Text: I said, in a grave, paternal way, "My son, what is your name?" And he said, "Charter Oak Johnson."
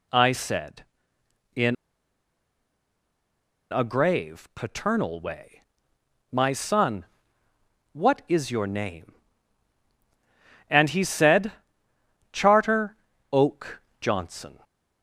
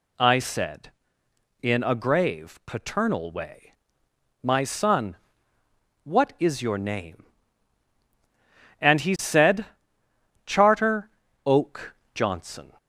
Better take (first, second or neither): second